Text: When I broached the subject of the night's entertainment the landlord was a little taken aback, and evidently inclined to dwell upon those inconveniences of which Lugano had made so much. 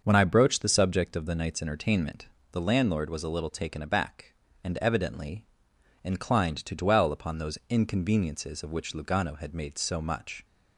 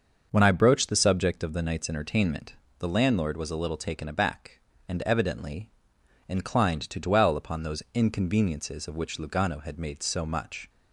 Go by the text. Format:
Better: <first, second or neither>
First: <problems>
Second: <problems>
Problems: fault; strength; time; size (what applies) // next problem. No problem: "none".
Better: neither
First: starts louder than the rest; until 1.0 s; 6.5 dB // pauses between "entertainment" and "the"; slight; at 2.2 s; 0.24 s long // pauses between "evidently" and "inclined"; noticeable; at 5.4 s; 0.56 s long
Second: starts louder than the rest; until 1.3 s; 6.5 dB // pauses between "entertainment" and "the"; slight; at 2.5 s; 0.24 s long // pauses between "evidently" and "inclined"; noticeable; at 5.7 s; 0.56 s long